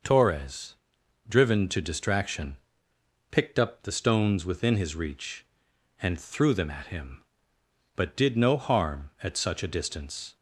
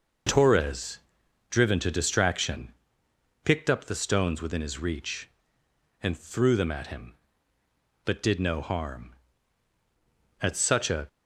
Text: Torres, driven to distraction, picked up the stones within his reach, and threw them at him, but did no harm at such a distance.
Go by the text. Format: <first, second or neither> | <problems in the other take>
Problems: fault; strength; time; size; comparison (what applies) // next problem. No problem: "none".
first | stops before "distance"; at 11.0 s